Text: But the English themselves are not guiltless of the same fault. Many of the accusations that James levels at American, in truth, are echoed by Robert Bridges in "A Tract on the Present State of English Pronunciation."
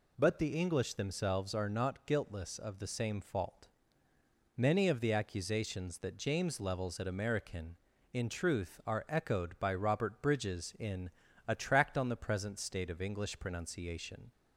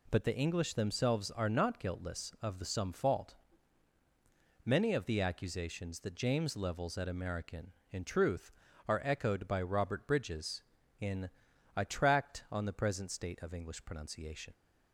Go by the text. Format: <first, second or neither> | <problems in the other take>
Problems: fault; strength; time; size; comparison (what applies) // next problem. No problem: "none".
first | says "some" for "same"; at 2.6 s // pauses between "in" and "A"; noticeable; at 11.2 s; 0.46 s long; also in the first